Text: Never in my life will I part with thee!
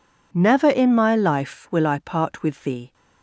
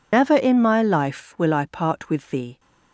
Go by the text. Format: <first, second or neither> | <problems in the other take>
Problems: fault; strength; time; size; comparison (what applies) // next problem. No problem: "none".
first | loses the start of "Never"; at 0.1 s; 130 ms